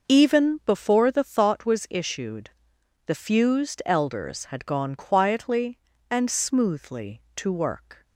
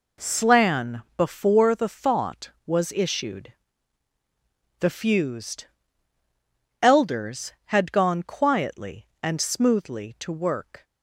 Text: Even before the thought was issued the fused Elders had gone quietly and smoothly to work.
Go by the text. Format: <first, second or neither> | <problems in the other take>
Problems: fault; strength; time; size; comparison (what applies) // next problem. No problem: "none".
first | says "Slan" for "Even"; at 0.2 s // pauses between "issued" and "the"; strong; at 3.5 s; 1.2 s long; noticeable in the first // pauses between "fused" and "Elders"; at 5.6 s; 1.1 s long